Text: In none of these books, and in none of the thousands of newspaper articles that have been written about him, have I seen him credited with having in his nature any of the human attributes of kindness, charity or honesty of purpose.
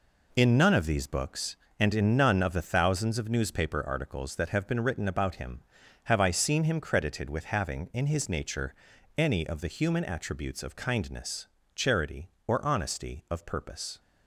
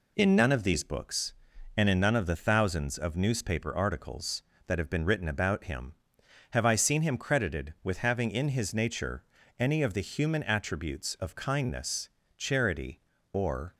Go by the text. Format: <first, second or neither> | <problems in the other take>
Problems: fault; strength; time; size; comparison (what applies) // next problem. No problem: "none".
first | pauses between "nature" and "any"; slight; at 9.2 s; 0.34 s long; also in the first // stops before "honesty of purpose"; at 13.7 s